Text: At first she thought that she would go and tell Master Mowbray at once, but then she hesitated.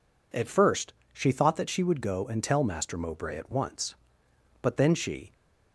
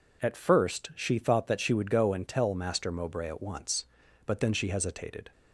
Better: second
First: pauses between "first" and "she"; slight; at 0.9 s; 0.18 s long // stops before "hesitated"; at 5.3 s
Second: none

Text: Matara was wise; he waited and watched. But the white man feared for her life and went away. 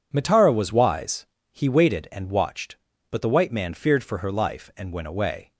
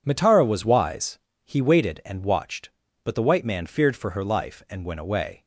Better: neither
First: none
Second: none

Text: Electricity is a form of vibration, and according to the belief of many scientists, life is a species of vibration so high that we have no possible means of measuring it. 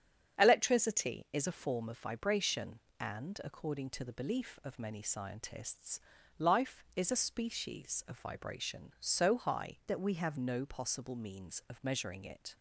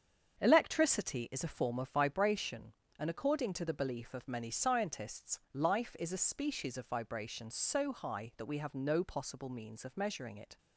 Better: second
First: starts louder than the rest; strong; until 1.4 s; 8 dB // changes voice from "that" to "have"; from 9.8 to 10.3 s; 0.5 s long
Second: starts louder than the rest; strong; until 1.4 s; 7.5 dB

